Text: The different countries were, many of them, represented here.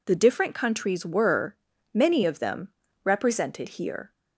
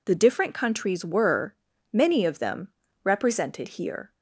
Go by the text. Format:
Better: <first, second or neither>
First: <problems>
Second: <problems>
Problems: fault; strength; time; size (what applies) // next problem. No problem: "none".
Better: neither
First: none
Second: none